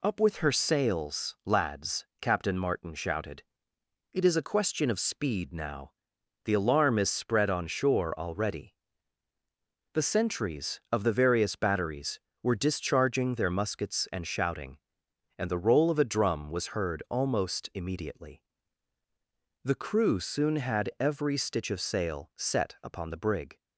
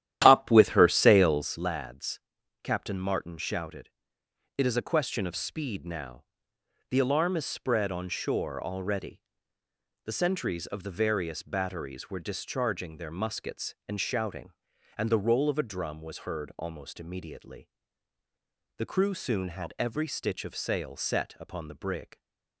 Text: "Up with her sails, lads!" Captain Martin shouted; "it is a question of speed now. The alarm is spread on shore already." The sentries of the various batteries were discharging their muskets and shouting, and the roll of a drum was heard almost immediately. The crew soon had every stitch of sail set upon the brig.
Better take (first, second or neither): first